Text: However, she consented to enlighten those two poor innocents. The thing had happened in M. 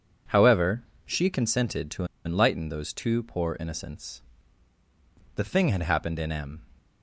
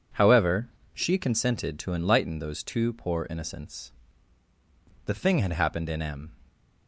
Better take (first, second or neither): second